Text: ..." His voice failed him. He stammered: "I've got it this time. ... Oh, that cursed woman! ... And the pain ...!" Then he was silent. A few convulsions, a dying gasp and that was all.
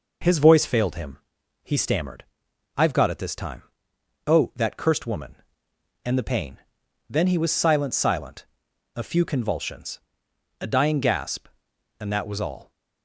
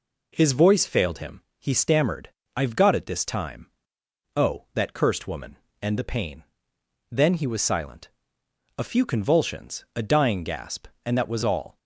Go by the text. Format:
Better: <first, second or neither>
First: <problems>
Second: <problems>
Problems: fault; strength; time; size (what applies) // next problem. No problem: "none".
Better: second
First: says "silent" twice; at 7.9 s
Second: none